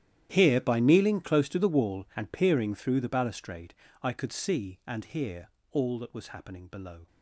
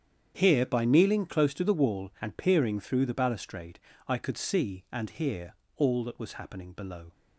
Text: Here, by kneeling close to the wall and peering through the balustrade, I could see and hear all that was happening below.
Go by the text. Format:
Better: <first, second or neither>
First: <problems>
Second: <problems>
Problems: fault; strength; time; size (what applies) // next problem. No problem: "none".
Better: second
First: gets quieter; strong; throughout; 18.5 dB // starts louder than the rest; strong; until 1.3 s; 11 dB // pauses between "hear" and "all"; slight; at 5.4 s; 0.24 s long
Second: starts louder than the rest; strong; until 1.3 s; 8.5 dB // pauses between "hear" and "all"; slight; at 5.5 s; 0.24 s long